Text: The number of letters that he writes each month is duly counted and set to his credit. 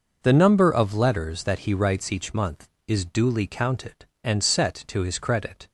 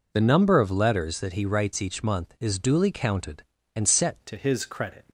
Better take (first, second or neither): first